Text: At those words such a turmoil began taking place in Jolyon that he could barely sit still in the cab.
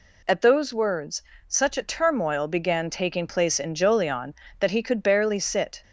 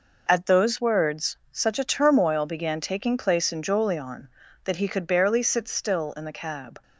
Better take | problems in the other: second | pauses between "words" and "such"; slight; at 1.2 s; 0.28 s long; slight in the second // stops before "still in the cab"; at 5.8 s

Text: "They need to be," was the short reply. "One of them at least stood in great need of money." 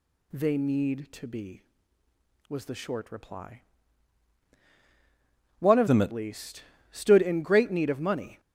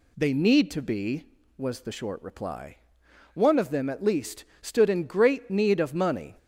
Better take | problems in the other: second | changes voice from "them" to "at"; from 5.8 to 6.1 s; 0.3 s long // pauses between "least" and "stood"; slight; at 6.6 s; 0.28 s long; slight in the second

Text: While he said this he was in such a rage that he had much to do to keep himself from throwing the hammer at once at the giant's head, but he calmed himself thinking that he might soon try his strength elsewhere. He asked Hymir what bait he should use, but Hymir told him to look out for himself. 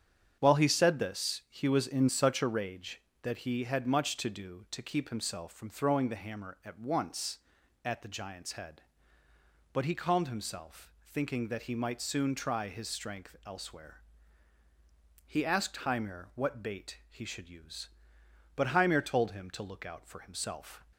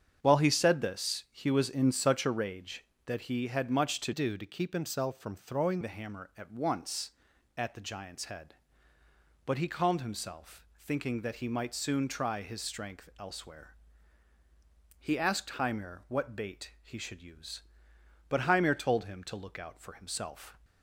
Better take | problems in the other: first | starts louder than the rest; strong; until 1.2 s; 7.5 dB; strong in the first // changes voice from "do" to "throwing"; from 4.1 to 5.7 s; 1.6 s long

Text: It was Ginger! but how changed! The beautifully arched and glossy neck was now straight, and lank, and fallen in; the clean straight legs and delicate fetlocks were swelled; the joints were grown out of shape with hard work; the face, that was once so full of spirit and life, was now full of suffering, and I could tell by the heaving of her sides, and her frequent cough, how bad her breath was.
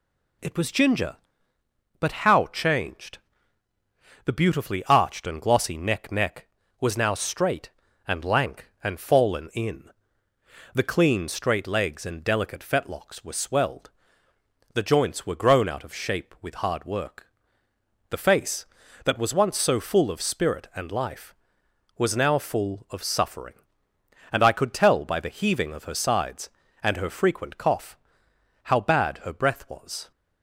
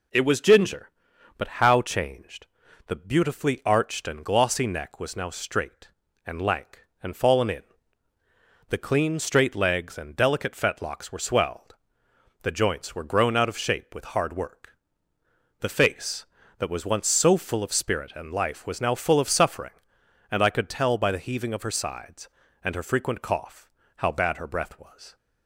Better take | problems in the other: second | says "neck" twice; at 6.1 s

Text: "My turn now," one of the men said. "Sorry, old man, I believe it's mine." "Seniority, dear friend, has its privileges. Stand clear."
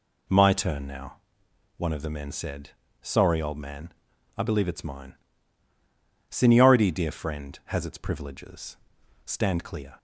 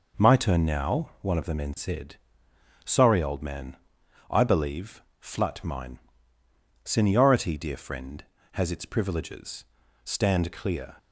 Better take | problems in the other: first | says "flut" for "it's"; at 5.1 s

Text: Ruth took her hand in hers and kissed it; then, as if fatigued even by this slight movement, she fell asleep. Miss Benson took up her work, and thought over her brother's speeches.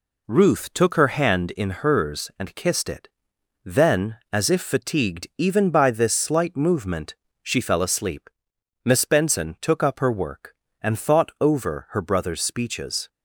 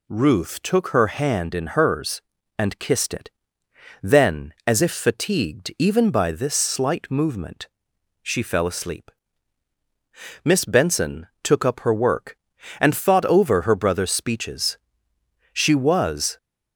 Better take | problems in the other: first | goes on to say "She was"; noticeable; from 15.5 s on; 0.84 s long

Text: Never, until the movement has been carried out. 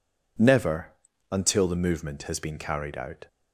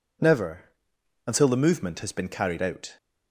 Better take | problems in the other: neither | none

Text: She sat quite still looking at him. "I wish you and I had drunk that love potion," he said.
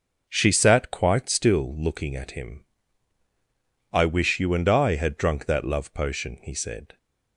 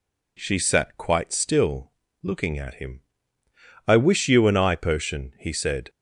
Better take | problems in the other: first | pauses between "still" and "looking"; slight; at 1.8 s; 0.32 s long // skips "had drunk that love"; at 4.7 s

